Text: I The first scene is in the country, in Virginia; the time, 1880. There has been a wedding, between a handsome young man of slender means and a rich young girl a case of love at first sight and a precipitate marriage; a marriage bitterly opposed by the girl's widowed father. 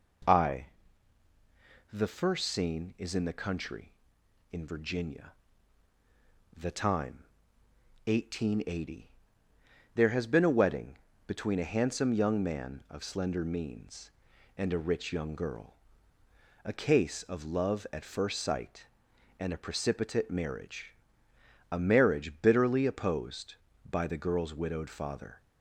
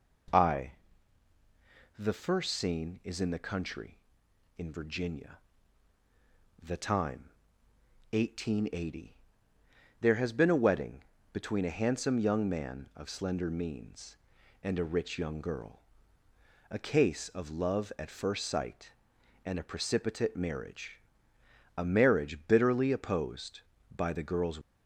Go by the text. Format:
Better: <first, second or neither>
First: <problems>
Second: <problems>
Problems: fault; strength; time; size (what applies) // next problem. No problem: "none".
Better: first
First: pauses between "I" and "The"; at 0.6 s; 1.2 s long // pauses between "girl" and "a"; noticeable; at 15.7 s; 0.92 s long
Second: pauses between "I" and "The"; at 0.7 s; 1.2 s long // pauses between "girl" and "a"; noticeable; at 15.7 s; 0.92 s long // stops before "widowed father"; at 24.6 s